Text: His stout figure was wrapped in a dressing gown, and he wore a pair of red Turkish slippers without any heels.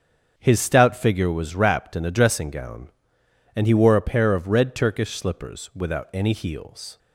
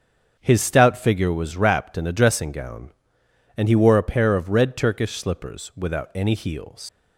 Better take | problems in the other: first | starts louder than the rest; until 1.4 s; 7 dB; strong in the first // leaves "heels" unfinished; at 6.8 s; 105 ms

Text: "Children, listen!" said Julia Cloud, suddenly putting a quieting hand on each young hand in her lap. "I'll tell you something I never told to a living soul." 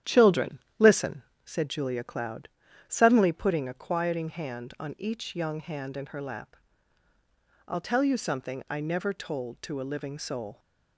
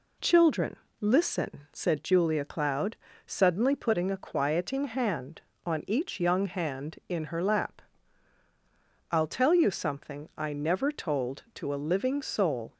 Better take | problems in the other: second | starts louder than the rest; strong; until 1.2 s; 10.5 dB

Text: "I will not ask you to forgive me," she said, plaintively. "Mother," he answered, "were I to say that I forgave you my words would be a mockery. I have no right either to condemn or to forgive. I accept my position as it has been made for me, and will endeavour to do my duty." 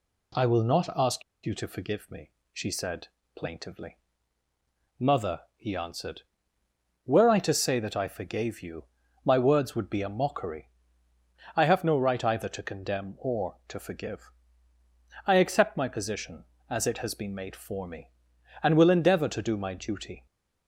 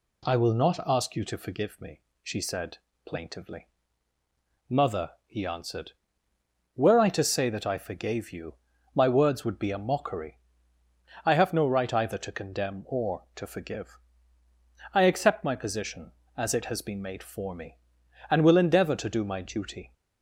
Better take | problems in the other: second | pauses between "ask" and "you"; slight; at 1.2 s; 0.22 s long // pauses between "you" and "my"; at 8.8 s; 0.42 s long; also in the second

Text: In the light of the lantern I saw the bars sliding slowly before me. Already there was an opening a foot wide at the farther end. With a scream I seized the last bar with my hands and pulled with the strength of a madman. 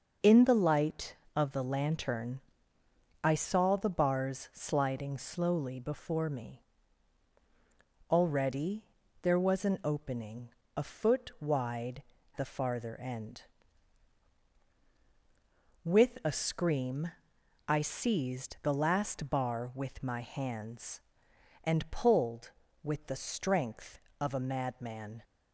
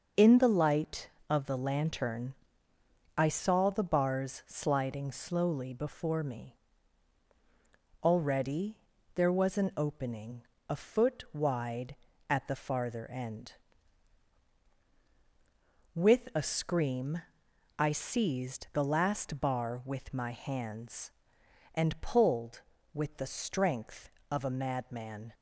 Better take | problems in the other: second | starts louder than the rest; noticeable; until 1.4 s; 6 dB; noticeable in the second // pauses between "lantern" and "I"; noticeable; at 2.4 s; 0.82 s long; noticeable in the second // pauses between "Already" and "there"; at 8.8 s; 0.38 s long; also in the second // pauses between "opening" and "a"; slight; at 10.4 s; 0.28 s long; slight in the second // skips "at"; at 12.1 s // pauses between "scream" and "I"; noticeable; at 17.1 s; 0.58 s long; noticeable in the second

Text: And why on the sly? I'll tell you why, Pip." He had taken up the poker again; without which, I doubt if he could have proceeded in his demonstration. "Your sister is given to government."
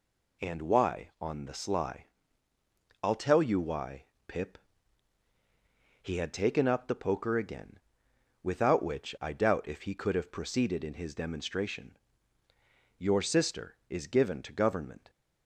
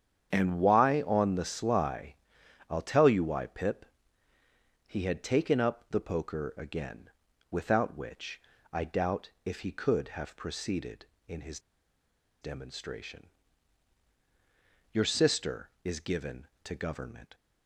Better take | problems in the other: first | starts louder than the rest; strong; until 1.3 s; 8.5 dB // pauses between "his" and "demonstration"; noticeable; at 11.5 s; 0.82 s long

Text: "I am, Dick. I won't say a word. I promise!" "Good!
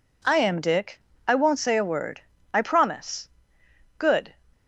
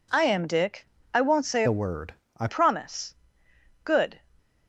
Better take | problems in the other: first | changes voice from "a" to "I"; from 1.6 to 2.4 s; 0.8 s long

